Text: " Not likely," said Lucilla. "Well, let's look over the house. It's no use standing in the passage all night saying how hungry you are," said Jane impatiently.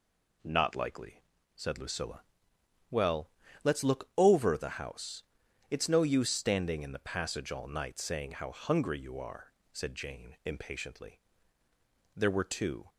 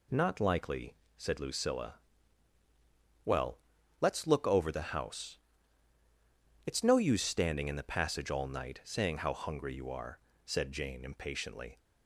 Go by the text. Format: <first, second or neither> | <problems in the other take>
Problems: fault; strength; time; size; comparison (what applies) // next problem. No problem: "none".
second | goes on to say "There were two"; noticeable; from 12.1 s on; 0.74 s long